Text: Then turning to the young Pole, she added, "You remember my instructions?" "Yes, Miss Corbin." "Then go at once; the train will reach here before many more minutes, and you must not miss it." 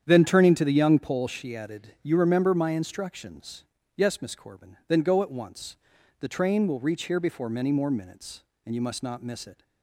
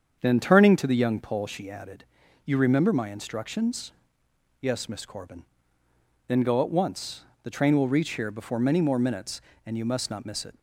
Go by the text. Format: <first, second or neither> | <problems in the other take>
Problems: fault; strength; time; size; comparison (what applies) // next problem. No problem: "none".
neither | starts louder than the rest; strong; the same in both